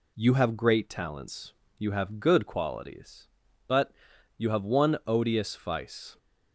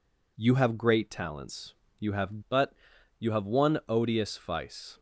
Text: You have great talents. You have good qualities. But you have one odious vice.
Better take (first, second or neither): first